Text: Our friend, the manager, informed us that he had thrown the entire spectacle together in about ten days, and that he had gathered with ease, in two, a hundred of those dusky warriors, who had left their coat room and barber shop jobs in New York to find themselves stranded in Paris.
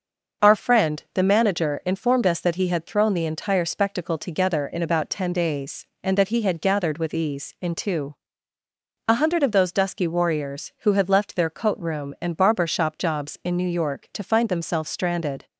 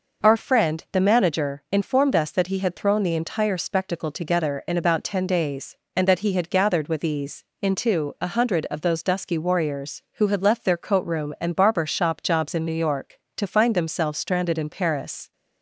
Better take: second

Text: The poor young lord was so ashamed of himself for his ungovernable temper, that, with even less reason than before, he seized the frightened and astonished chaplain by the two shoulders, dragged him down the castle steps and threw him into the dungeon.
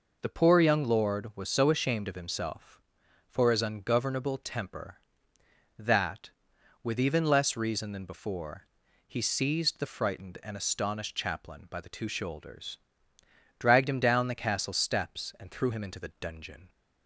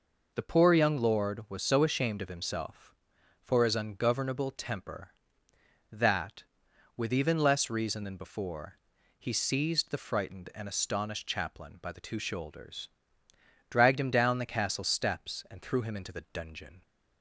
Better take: neither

